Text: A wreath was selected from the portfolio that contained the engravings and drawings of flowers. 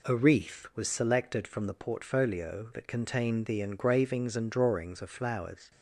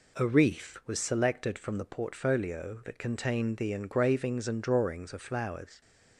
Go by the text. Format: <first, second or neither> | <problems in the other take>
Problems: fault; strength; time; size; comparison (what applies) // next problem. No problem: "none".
neither | none